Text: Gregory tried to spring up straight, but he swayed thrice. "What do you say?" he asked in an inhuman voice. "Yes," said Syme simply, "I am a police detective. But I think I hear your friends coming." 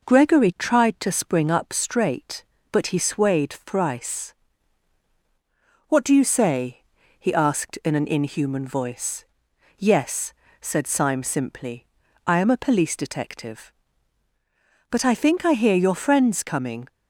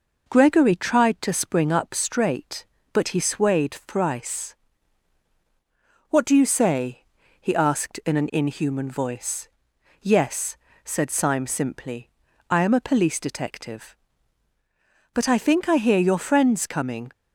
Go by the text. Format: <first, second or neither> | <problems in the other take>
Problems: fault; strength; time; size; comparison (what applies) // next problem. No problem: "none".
neither | none